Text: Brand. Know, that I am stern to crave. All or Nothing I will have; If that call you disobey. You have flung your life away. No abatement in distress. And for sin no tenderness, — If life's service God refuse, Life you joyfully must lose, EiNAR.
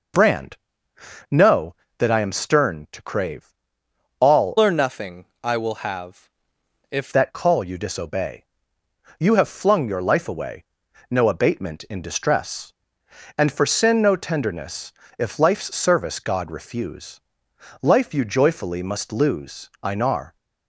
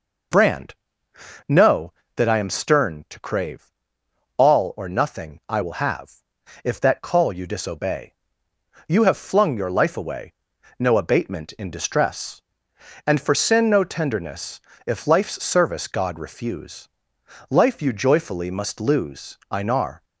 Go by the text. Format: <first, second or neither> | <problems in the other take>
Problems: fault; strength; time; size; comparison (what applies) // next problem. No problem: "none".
second | changes voice from "or" to "If"; from 4.5 to 7.1 s; 2.6 s long // pauses between "Nothing" and "I"; slight; at 5.2 s; 0.18 s long